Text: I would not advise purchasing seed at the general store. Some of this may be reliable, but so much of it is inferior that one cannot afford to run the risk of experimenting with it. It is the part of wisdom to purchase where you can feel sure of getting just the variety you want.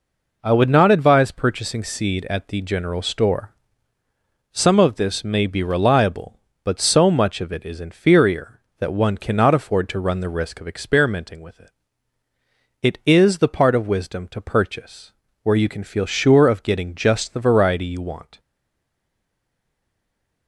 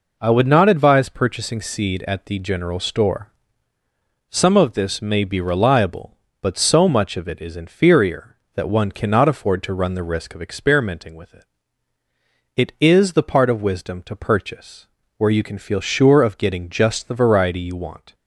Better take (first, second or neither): second